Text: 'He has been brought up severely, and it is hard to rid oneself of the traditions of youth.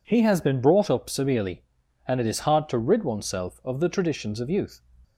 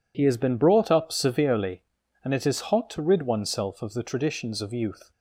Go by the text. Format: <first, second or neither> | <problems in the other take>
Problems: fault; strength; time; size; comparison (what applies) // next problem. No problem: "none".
first | says "hot" for "hard"; at 2.7 s